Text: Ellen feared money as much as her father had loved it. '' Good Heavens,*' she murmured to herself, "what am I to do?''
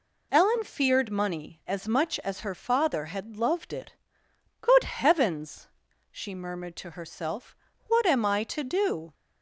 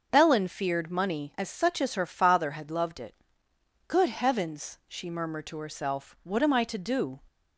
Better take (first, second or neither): first